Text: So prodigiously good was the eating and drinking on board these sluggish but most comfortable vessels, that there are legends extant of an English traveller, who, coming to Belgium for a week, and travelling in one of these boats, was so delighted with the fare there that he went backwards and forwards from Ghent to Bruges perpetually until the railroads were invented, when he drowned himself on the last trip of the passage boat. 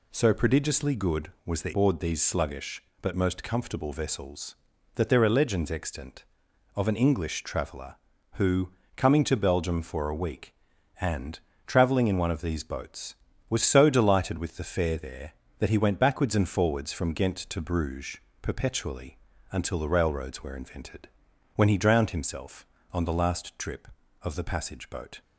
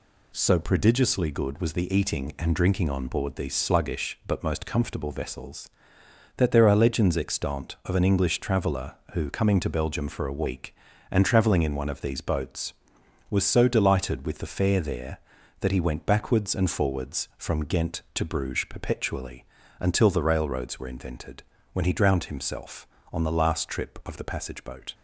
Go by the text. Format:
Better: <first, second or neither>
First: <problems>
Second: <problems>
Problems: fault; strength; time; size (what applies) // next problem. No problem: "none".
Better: second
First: skips "eating and drinking on"; at 1.7 s // pauses between "and" and "travelling"; slight; at 11.3 s; 0.30 s long // pauses between "Bruges" and "perpetually"; slight; at 18.1 s; 0.24 s long // pauses between "perpetually" and "until"; slight; at 19.1 s; 0.34 s long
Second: pauses between "perpetually" and "until"; slight; at 19.4 s; 0.36 s long